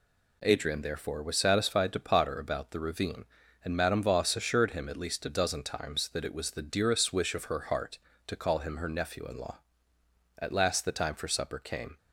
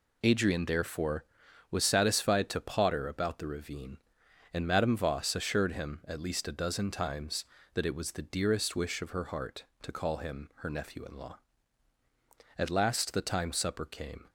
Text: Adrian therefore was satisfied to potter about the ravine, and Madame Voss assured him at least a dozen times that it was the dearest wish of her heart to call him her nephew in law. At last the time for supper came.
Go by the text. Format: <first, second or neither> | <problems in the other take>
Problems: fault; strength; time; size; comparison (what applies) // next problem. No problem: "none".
first | skips "for"; at 13.5 s